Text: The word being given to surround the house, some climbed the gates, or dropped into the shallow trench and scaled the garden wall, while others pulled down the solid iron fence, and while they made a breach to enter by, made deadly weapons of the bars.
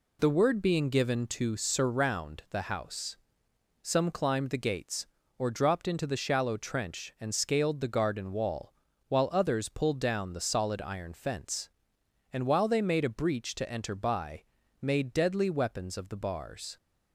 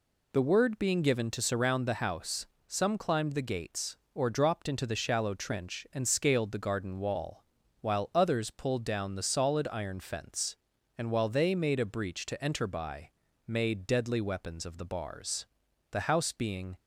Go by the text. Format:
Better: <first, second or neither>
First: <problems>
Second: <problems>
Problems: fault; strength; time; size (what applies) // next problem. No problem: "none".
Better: first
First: none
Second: goes on to say "The house being"; noticeable; from 15.9 s on; 0.86 s long